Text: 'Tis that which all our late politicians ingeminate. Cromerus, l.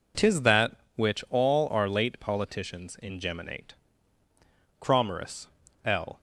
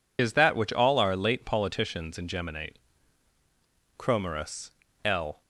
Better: first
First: none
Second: loses the start of "Tis"; at 0.1 s; 110 ms

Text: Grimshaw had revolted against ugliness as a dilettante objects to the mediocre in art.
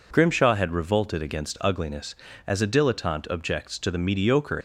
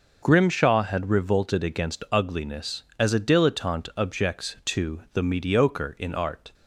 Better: second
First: stops before "in art"; at 4.5 s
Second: none

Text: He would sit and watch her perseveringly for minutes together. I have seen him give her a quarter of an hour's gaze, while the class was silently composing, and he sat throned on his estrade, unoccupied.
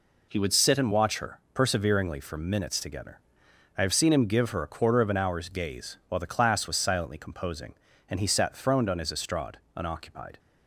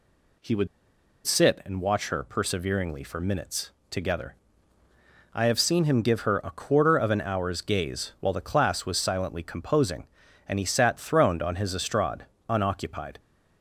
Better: first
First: none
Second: pauses between "would" and "sit"; noticeable; at 0.6 s; 0.59 s long // pauses between "minutes" and "together"; slight; at 3.7 s; 0.20 s long

